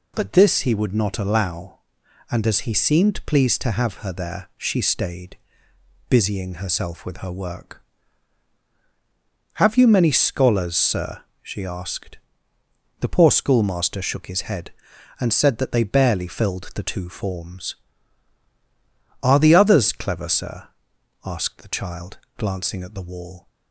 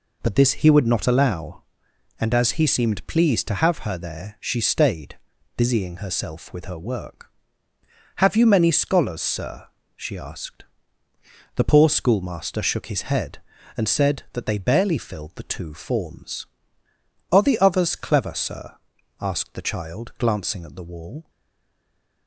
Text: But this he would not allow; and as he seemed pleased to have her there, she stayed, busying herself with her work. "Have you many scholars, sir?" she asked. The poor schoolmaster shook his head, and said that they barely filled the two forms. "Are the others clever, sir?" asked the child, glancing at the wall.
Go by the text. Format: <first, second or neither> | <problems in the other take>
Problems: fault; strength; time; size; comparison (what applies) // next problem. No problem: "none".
first | stays silent after the last word; from 21.2 s on; 1.0 s long